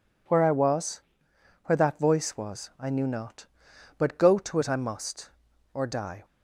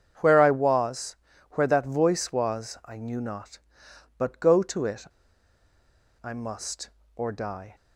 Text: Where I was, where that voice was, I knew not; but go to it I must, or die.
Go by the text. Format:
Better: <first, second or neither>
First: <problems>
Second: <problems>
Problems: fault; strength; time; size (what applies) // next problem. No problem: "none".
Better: first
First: none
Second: starts louder than the rest; strong; until 1.5 s; 7.5 dB // pauses between "it" and "I"; at 5.0 s; 1.1 s long